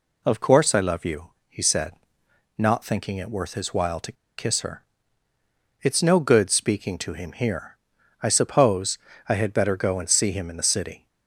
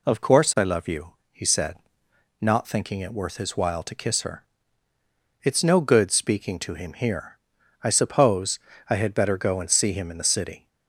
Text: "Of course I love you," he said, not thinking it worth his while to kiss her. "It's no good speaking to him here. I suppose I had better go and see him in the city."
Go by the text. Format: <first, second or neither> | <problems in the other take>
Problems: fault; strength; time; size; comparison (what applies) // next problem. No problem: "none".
second | pauses between "to" and "kiss"; slight; at 4.1 s; 0.25 s long // pauses between "suppose" and "I"; slight; at 8.9 s; 0.28 s long; slight in the second